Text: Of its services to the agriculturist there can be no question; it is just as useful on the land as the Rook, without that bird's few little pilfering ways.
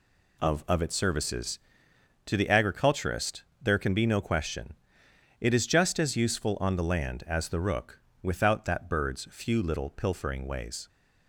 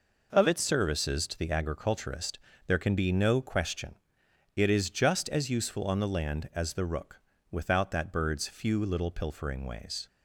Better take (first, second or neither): second